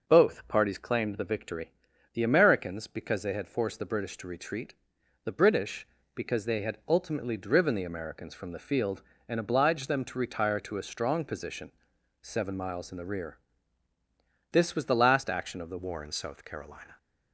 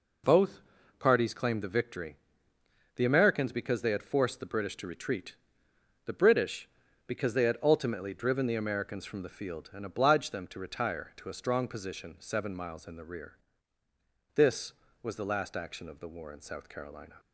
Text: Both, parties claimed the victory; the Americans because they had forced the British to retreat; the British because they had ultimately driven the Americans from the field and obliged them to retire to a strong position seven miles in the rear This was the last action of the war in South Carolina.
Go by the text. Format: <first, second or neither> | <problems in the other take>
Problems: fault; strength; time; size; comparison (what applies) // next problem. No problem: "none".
second | pauses between "position" and "seven"; noticeable; at 11.7 s; 0.48 s long // pauses between "rear" and "This"; at 13.3 s; 1.1 s long; also in the second // changes voice at "war"; from 15.7 s on; 1.2 s long